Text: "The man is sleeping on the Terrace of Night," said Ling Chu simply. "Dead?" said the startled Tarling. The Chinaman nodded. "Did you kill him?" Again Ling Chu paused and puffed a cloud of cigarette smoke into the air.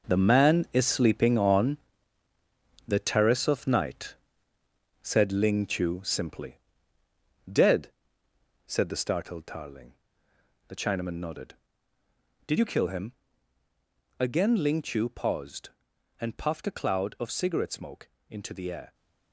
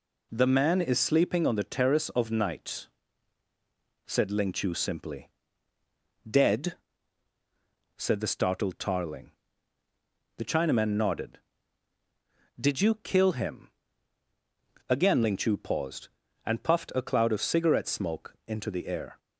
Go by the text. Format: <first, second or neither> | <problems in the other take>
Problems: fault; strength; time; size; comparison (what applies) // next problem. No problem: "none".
second | gets quieter; strong; throughout; 10.5 dB // pauses between "on" and "the"; at 1.7 s; 1.1 s long // pauses between "smoke" and "into"; slight; at 18.0 s; 0.22 s long